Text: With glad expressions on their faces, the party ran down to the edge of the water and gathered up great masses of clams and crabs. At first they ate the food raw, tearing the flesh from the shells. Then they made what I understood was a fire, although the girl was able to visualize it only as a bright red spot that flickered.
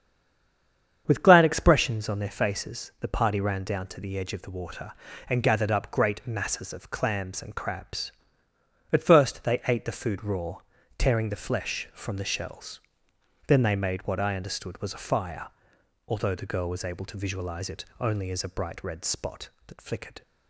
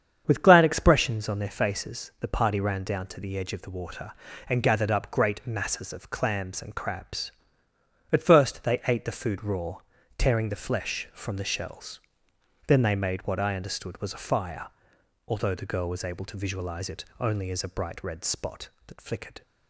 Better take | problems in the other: second | stays silent before the first word; until 1.0 s; 1.0 s long // starts louder than the rest; strong; until 2.0 s; 8 dB; strong in the second // pauses between "it" and "only"; slight; at 17.8 s; 0.16 s long; slight in the second

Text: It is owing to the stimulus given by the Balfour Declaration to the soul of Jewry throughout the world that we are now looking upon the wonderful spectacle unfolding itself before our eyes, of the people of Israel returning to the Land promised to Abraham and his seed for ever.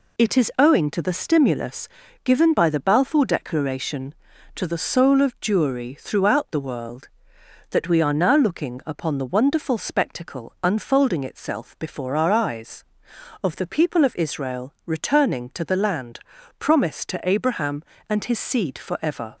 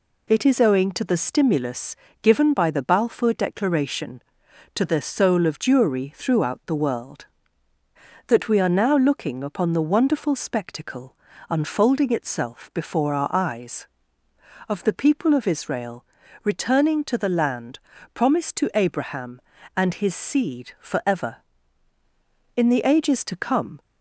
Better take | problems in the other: first | pauses between "stimulus" and "given"; slight; at 1.9 s; 0.26 s long; slight in the first // pauses between "spectacle" and "unfolding"; slight; at 11.1 s; 0.32 s long // pauses between "Israel" and "returning"; at 16.0 s; 0.40 s long // pauses between "Land" and "promised"; slight; at 17.7 s; 0.34 s long; also in the first // goes on to say "In the ages to come"; noticeable; from 22.5 s on; 1.2 s long

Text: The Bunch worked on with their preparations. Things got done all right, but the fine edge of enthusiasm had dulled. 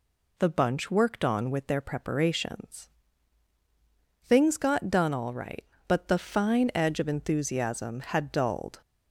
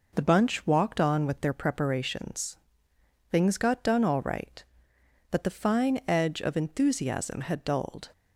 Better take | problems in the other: first | says "walked" for "worked"; at 0.6 s

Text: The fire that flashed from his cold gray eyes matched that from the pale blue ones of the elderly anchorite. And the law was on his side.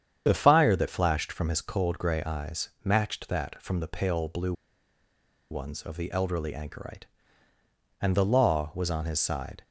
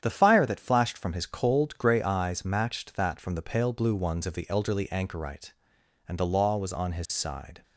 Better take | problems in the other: second | starts louder than the rest; strong; until 1.2 s; 8.5 dB; strong in the second // pauses between "eyes" and "matched"; slight; at 2.6 s; 0.16 s long // pauses between "blue" and "ones"; noticeable; at 4.5 s; 0.97 s long

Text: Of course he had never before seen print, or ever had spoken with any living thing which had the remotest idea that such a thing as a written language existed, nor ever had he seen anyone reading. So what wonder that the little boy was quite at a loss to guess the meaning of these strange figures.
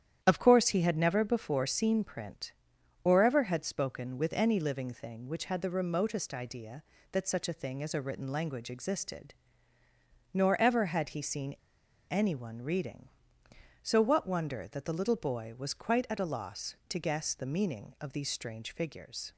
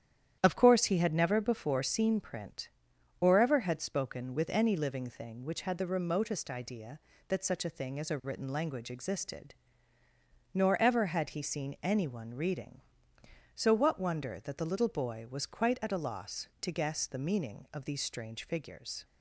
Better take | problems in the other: second | starts louder than the rest; strong; until 1.2 s; 10 dB; strong in the second // pauses between "seen" and "anyone"; noticeable; at 11.5 s; 0.52 s long

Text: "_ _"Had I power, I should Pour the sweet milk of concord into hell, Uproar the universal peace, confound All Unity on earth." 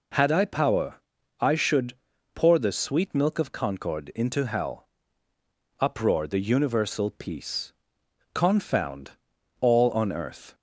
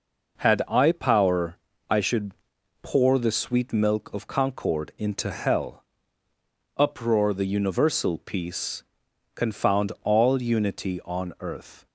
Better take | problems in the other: second | pauses between "should" and "Pour"; at 1.9 s; 0.40 s long; noticeable in the second // pauses between "confound" and "All"; noticeable; at 9.1 s; 0.48 s long // skips "Unity"; at 9.9 s

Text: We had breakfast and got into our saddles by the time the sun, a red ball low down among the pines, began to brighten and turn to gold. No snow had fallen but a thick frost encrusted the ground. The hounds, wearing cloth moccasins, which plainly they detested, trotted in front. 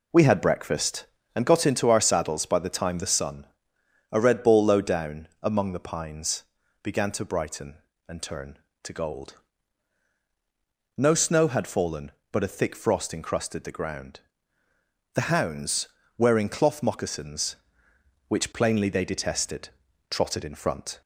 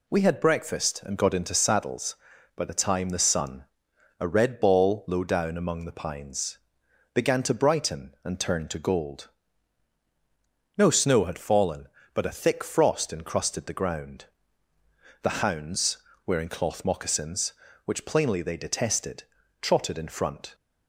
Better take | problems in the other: first | skips "our"; at 1.5 s

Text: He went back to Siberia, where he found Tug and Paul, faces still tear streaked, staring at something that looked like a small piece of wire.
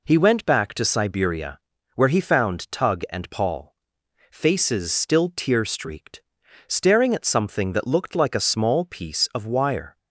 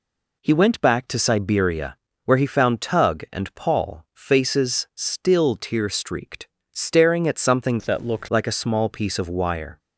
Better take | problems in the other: first | changes voice from "that" to "looked"; from 7.8 to 8.2 s; 0.4 s long

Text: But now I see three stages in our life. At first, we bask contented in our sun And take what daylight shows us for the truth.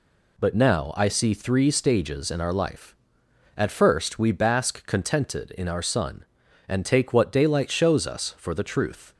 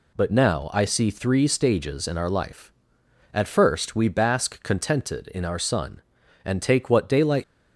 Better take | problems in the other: first | stops before "shows us for the truth"; at 7.4 s

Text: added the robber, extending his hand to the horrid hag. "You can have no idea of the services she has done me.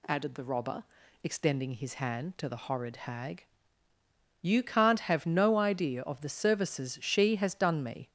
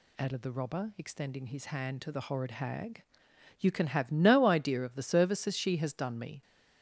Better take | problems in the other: second | says "can't" for "can"; at 4.6 s

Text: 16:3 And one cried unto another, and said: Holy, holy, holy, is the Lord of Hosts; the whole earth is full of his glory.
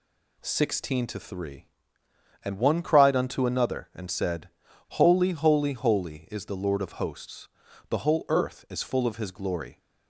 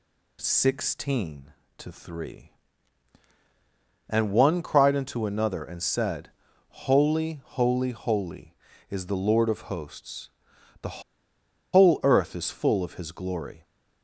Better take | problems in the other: first | pauses between "the" and "whole"; noticeable; at 11.0 s; 0.71 s long

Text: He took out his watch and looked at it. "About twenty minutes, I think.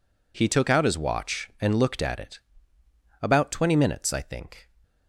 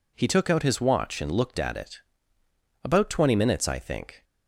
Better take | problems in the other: neither | none

